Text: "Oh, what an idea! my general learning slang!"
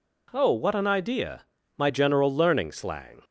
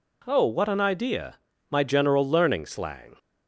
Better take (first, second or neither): neither